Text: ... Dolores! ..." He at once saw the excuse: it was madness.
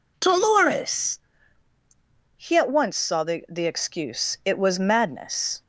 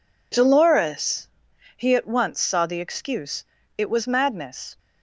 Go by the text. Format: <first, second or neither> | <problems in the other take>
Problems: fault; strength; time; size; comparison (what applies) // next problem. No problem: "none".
second | says "the" twice; at 3.4 s